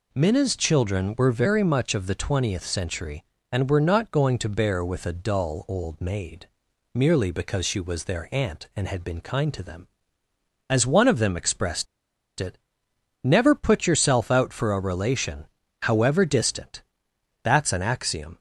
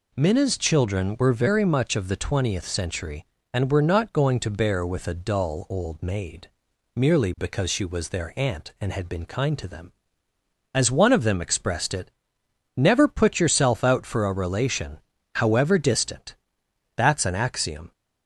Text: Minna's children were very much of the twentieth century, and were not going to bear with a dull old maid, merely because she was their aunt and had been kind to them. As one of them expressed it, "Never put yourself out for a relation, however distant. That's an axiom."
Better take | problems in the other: second | pauses between "expressed" and "it"; noticeable; at 11.8 s; 0.54 s long

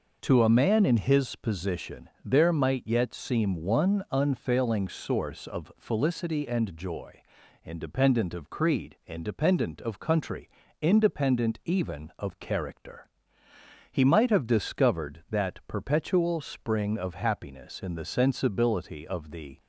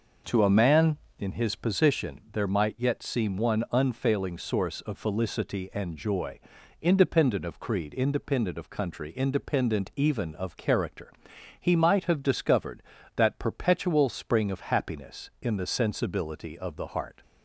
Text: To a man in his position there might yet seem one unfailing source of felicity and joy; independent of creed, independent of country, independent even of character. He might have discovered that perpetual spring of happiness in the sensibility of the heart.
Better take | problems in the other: second | pauses between "position" and "there"; slight; at 2.0 s; 0.16 s long // stops before "heart"; at 19.5 s

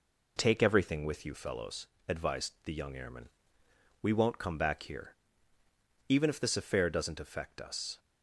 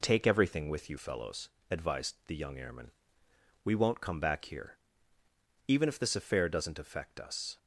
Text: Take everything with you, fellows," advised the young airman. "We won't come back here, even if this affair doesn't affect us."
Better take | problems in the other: neither | none

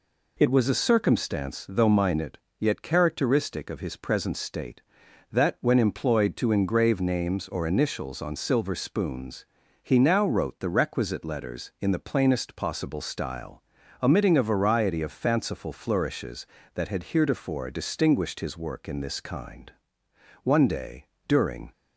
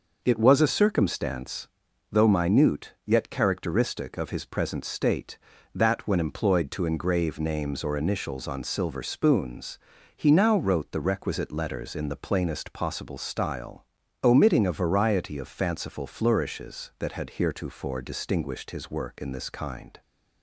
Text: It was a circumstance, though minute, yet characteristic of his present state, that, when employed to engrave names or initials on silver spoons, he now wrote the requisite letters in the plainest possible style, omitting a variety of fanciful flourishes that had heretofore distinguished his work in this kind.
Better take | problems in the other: second | goes on to say "One day during"; noticeable; from 20.4 s on; 1.2 s long

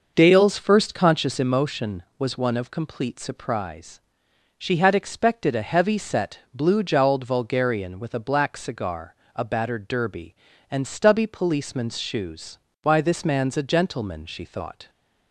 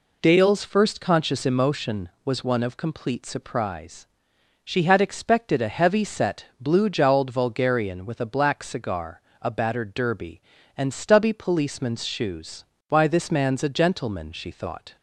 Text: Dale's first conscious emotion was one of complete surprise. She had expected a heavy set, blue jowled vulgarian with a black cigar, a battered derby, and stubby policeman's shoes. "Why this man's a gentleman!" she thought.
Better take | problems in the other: second | starts louder than the rest; noticeable; until 1.3 s; 6 dB

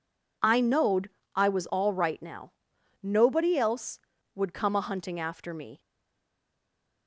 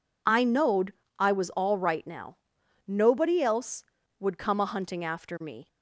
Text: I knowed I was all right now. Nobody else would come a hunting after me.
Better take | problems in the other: second | pauses between "knowed" and "I"; slight; at 1.0 s; 0.26 s long; slight in the second // stays silent after the last word; noticeable; from 5.7 s on; 1.3 s long

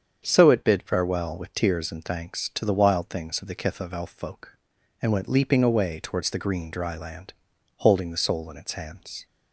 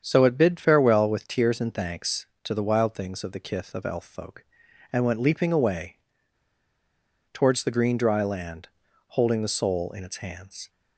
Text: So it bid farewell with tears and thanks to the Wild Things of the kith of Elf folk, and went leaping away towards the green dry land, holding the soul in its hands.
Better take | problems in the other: first | starts louder than the rest; strong; until 1.0 s; 8 dB; strong in the first // pauses between "away" and "towards"; strong; at 5.9 s; 1.3 s long

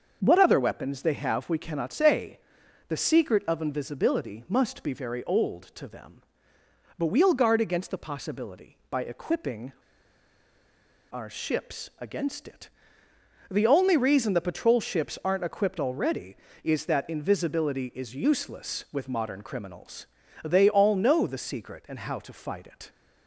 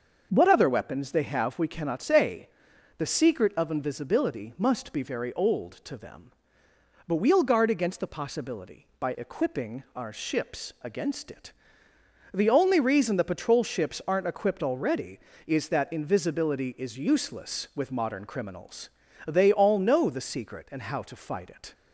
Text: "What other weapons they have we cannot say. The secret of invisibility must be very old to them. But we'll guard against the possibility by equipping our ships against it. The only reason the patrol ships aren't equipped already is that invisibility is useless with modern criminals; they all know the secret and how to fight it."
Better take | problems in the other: second | starts louder than the rest; until 1.2 s; 6.5 dB; also in the second // pauses between "equipping" and "our"; strong; at 9.7 s; 1.3 s long

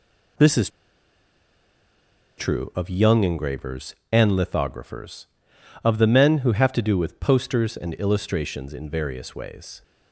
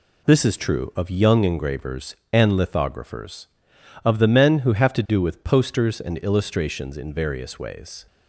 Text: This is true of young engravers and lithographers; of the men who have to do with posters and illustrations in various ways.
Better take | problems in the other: second | pauses between "is" and "true"; strong; at 0.6 s; 1.6 s long

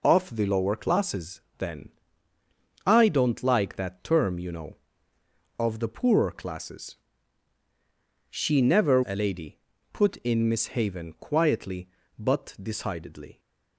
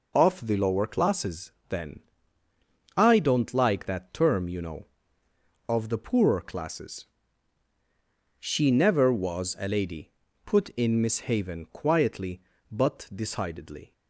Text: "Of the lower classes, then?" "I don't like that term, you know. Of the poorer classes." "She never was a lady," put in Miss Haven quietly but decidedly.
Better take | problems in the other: second | skips "was"; at 9.0 s

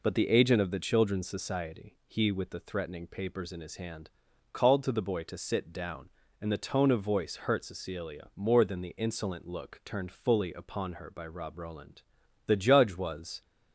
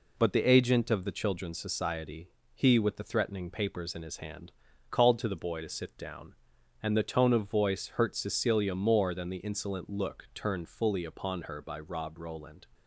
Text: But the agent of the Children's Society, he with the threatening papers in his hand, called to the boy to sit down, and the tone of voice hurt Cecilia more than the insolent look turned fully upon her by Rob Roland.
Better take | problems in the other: second | goes on to say "The judge was"; noticeable; from 12.4 s on; 0.94 s long

